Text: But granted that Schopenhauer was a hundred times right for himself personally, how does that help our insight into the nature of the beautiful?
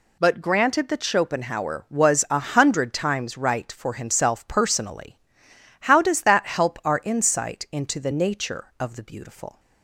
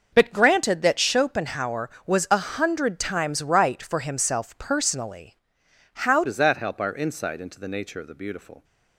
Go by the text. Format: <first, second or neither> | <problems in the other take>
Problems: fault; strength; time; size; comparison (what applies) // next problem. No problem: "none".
first | starts louder than the rest; noticeable; until 1.1 s; 6 dB // changes voice at "does"; from 6.2 s on; 2.4 s long